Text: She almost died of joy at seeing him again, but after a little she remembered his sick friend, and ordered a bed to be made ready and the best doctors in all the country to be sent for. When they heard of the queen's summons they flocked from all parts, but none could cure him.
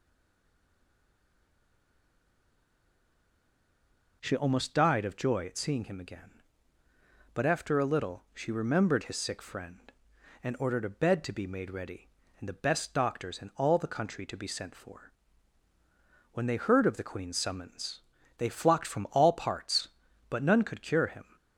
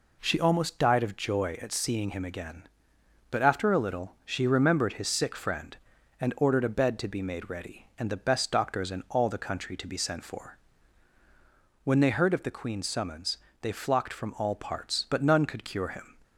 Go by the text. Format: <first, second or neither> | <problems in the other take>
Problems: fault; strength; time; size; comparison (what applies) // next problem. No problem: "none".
second | stays silent before the first word; strong; until 4.2 s; 4.2 s long // pauses between "summons" and "they"; slight; at 18.0 s; 0.36 s long; slight in the second